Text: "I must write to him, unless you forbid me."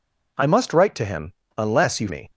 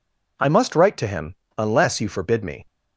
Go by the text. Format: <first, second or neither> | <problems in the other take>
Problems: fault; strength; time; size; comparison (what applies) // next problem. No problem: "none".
second | skips "forbid"; at 2.0 s